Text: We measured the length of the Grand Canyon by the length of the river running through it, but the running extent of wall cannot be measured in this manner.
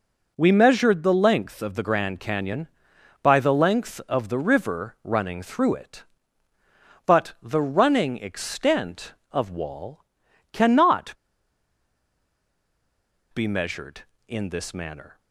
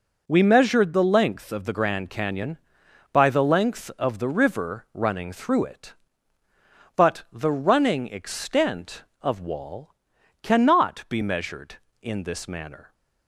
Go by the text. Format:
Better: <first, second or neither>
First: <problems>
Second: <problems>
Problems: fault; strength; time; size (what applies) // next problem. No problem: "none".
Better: second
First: pauses between "wall" and "cannot"; noticeable; at 10.0 s; 0.50 s long // pauses between "cannot" and "be"; strong; at 11.1 s; 2.2 s long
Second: pauses between "wall" and "cannot"; noticeable; at 9.9 s; 0.50 s long